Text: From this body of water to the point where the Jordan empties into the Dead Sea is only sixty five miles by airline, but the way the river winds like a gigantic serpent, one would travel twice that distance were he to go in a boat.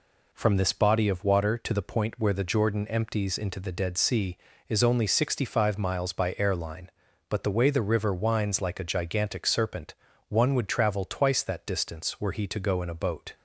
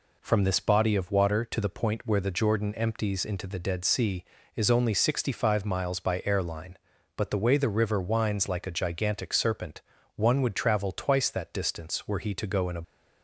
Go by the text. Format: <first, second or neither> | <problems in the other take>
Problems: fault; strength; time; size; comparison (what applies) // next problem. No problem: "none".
first | stops before "boat"; at 12.8 s